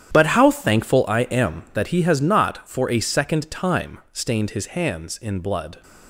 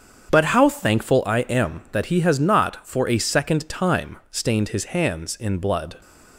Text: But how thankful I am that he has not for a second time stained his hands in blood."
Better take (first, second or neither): second